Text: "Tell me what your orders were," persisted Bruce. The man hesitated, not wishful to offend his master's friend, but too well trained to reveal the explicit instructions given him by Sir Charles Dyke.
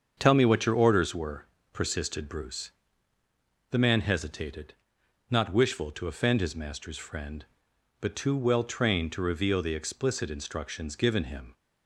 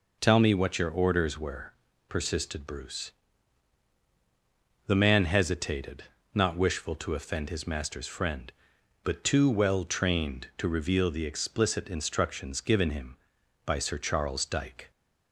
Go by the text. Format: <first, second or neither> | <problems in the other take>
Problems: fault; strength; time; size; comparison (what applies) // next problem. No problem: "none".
second | starts louder than the rest; until 1.2 s; 7 dB // stops before "by Sir Charles Dyke"; at 11.5 s